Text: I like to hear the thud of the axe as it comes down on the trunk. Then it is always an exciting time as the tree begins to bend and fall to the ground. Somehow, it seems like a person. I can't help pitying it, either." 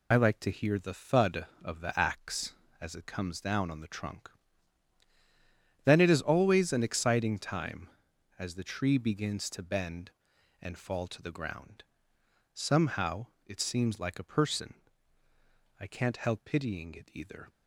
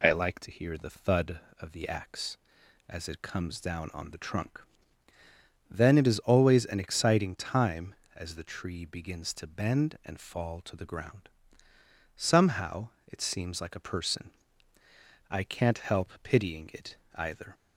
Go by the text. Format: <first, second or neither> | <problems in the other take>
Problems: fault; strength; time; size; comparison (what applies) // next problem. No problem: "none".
second | loses the start of "I"; at 0.1 s; 45 ms